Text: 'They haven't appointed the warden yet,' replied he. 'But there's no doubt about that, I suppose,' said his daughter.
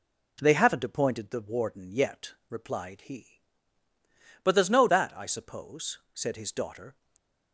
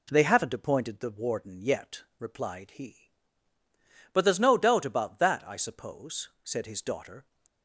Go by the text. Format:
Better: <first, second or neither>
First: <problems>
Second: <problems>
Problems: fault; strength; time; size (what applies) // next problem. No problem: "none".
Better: second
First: skips "doubt about"; at 4.8 s // stays silent after the last word; slight; from 6.9 s on; 0.6 s long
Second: none